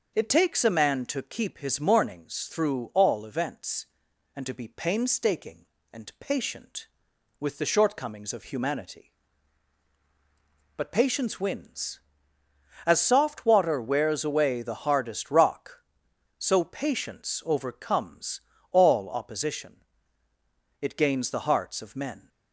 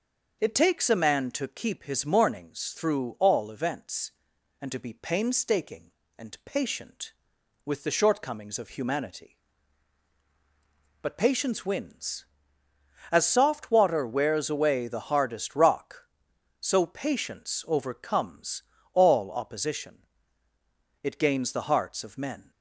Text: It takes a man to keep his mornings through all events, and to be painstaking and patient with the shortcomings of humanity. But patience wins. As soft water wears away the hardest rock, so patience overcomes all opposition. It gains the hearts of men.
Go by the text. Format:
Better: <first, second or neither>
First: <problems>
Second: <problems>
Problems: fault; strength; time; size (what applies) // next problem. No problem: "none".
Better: neither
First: pauses between "overcomes" and "all"; slight; at 18.4 s; 0.32 s long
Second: pauses between "overcomes" and "all"; slight; at 18.6 s; 0.32 s long